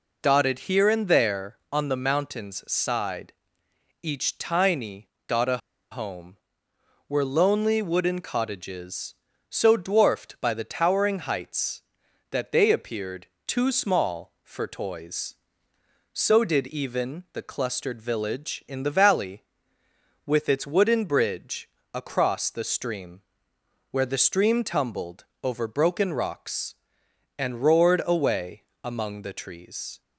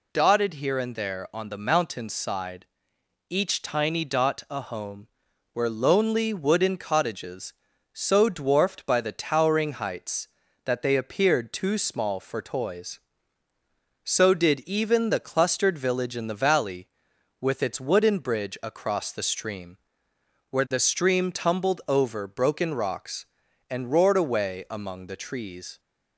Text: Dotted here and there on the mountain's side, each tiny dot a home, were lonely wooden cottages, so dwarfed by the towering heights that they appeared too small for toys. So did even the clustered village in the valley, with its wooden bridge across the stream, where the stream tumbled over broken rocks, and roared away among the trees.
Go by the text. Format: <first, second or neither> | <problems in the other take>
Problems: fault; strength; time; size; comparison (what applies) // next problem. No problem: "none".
second | pauses between "tiny" and "dot"; slight; at 5.0 s; 0.18 s long // pauses between "a" and "home"; slight; at 5.5 s; 0.32 s long // pauses between "appeared" and "too"; slight; at 13.2 s; 0.18 s long // pauses between "bridge" and "across"; slight; at 21.6 s; 0.24 s long // pauses between "tumbled" and "over"; slight; at 25.2 s; 0.18 s long // pauses between "away" and "among"; slight; at 28.6 s; 0.20 s long